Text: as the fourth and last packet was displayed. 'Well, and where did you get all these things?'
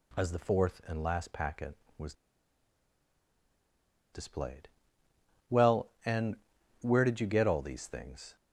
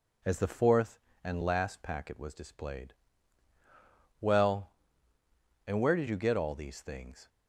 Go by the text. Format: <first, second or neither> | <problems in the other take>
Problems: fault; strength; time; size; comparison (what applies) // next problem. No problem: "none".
second | pauses between "was" and "displayed"; strong; at 2.1 s; 1.9 s long // pauses between "and" and "where"; noticeable; at 6.3 s; 0.46 s long